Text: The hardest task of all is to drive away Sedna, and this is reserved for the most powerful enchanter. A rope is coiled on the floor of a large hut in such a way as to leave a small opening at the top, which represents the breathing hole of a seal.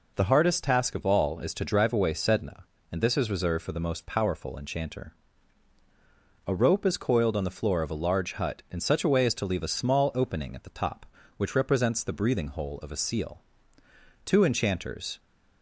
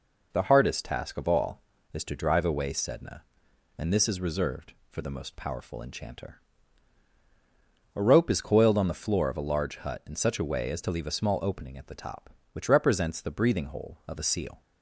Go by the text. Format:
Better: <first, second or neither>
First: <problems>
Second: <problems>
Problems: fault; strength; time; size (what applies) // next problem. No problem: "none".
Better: second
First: goes on to say "Two enchanters"; noticeable; from 14.2 s on; 0.94 s long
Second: none